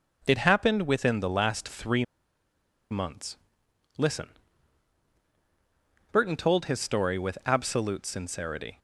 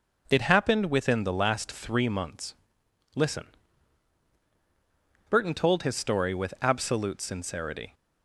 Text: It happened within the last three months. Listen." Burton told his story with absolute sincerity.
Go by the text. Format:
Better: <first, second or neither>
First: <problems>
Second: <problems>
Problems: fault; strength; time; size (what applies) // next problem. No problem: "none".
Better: second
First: pauses between "three" and "months"; noticeable; at 2.0 s; 0.86 s long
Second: none